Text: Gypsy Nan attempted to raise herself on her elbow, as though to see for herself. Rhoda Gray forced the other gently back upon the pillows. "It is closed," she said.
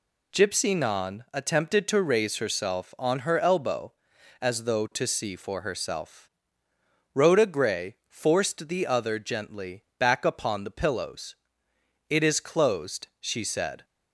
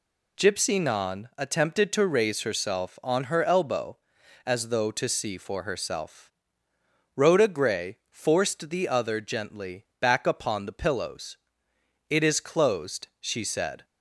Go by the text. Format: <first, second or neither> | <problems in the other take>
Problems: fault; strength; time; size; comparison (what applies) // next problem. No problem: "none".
neither | pauses between "gently" and "back"; slight; the same in both